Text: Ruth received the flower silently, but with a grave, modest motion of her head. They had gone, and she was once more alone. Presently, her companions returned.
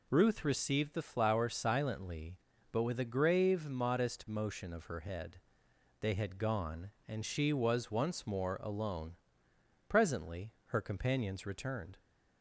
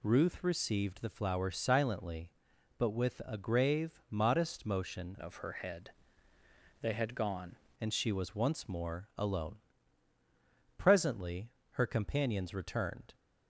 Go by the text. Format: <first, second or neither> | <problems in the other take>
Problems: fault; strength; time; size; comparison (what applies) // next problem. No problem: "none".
first | changes voice from "of" to "gone"; from 5.1 to 7.5 s; 2.4 s long